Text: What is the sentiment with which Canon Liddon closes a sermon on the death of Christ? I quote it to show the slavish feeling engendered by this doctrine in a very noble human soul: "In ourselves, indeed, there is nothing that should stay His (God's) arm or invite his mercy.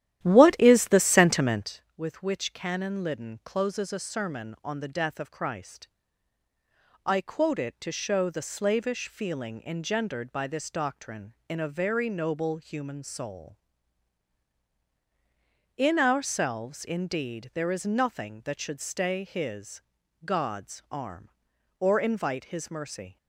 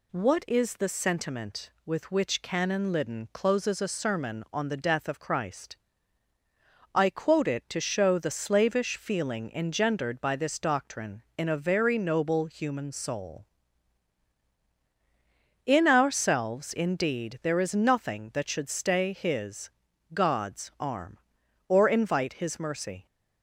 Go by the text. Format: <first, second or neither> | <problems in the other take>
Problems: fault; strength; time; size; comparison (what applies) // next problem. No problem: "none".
second | starts louder than the rest; strong; until 1.7 s; 12.5 dB